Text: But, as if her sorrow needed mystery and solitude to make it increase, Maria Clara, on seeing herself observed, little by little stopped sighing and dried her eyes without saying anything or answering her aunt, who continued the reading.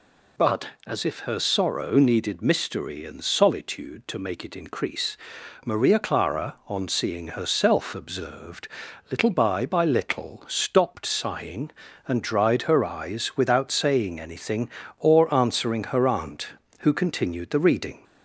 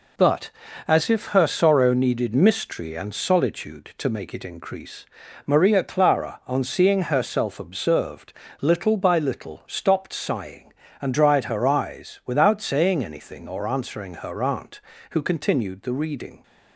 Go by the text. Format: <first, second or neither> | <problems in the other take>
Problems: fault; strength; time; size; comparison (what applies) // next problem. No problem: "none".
second | says "by" twice; at 9.6 s